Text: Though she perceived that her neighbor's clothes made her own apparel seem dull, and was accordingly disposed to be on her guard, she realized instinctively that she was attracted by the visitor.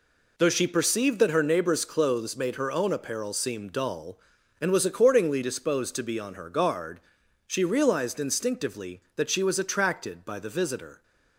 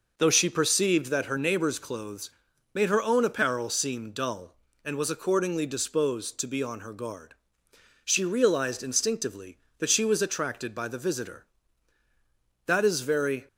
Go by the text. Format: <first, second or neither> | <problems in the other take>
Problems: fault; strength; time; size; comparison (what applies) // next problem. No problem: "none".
first | pauses between "clothes" and "made"; at 2.2 s; 0.44 s long // goes on to say "That is very"; noticeable; from 12.6 s on; 0.80 s long